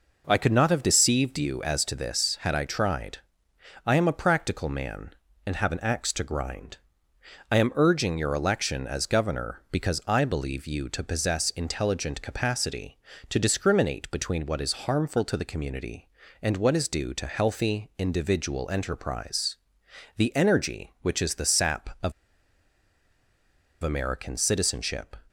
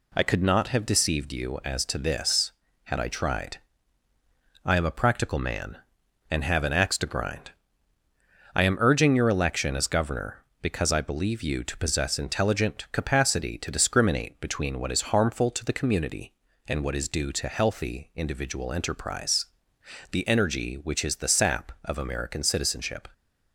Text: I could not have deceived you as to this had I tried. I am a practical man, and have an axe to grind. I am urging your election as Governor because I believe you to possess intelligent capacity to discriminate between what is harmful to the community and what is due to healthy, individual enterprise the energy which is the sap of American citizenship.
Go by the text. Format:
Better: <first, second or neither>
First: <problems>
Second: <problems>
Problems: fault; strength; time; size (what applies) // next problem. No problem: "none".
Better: second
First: pauses between "enterprise" and "the"; noticeable; at 19.5 s; 0.60 s long // pauses between "of" and "American"; strong; at 22.1 s; 1.7 s long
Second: pauses between "enterprise" and "the"; noticeable; at 19.4 s; 0.66 s long